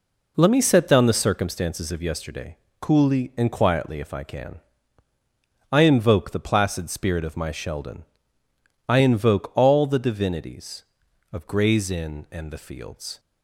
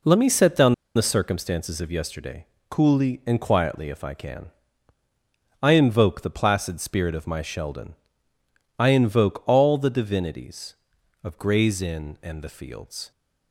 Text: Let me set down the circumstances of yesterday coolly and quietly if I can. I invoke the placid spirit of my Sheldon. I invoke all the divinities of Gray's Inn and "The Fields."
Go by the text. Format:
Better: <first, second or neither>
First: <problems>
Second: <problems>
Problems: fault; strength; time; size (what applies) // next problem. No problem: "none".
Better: first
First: pauses between "yesterday" and "coolly"; slight; at 2.5 s; 0.24 s long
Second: pauses between "down" and "the"; slight; at 0.7 s; 0.21 s long // pauses between "yesterday" and "coolly"; slight; at 2.4 s; 0.24 s long